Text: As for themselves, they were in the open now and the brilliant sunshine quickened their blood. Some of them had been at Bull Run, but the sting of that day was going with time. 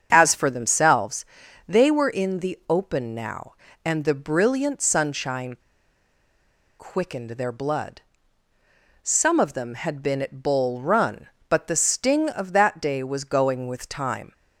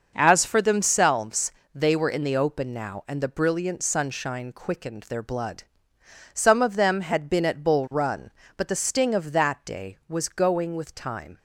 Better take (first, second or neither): second